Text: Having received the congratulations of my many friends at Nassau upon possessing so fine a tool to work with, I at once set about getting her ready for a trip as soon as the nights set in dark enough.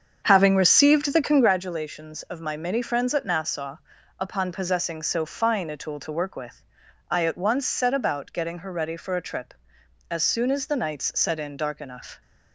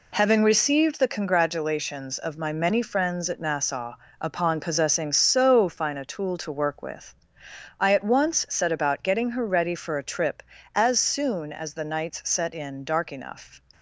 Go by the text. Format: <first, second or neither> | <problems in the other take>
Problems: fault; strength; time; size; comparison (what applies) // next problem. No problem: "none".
second | starts louder than the rest; strong; until 1.5 s; 7 dB // pauses between "Nassau" and "upon"; at 3.7 s; 0.42 s long; slight in the second